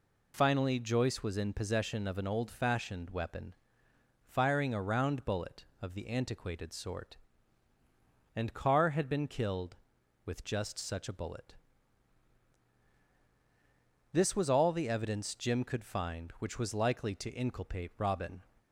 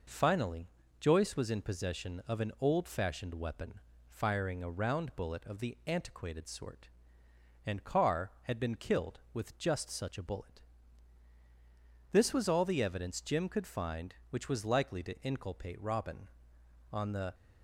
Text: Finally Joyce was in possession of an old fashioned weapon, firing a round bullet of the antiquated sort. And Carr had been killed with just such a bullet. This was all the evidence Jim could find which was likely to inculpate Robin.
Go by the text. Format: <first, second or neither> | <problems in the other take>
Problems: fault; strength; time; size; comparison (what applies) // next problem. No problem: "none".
first | pauses between "Finally" and "Joyce"; slight; at 0.6 s; 0.34 s long // goes on to say "On the"; slight; from 16.9 s on; 0.44 s long